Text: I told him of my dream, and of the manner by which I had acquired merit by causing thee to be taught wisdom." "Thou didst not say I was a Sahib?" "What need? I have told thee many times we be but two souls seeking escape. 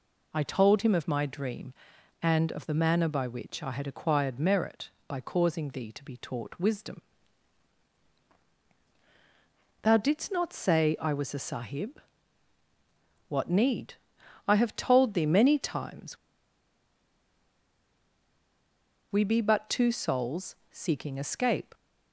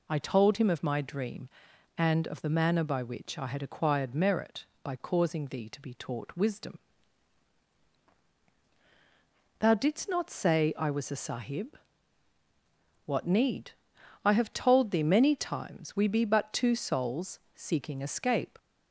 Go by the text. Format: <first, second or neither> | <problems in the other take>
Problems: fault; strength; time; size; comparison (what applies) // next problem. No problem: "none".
second | pauses between "times" and "we"; strong; at 16.1 s; 2.9 s long // pauses between "souls" and "seeking"; slight; at 20.5 s; 0.16 s long; slight in the second